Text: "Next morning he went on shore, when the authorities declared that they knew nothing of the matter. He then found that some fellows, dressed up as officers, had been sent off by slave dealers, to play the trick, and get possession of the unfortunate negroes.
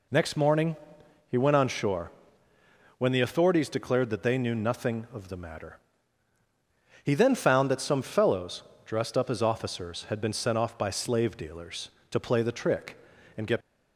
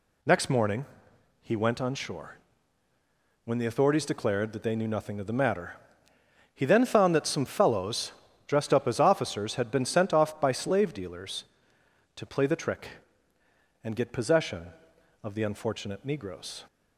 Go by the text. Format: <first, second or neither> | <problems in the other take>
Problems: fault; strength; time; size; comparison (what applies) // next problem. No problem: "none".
second | pauses between "morning" and "he"; noticeable; at 0.7 s; 0.52 s long; noticeable in the second // stops before "possession of the unfortunate negroes"; at 13.6 s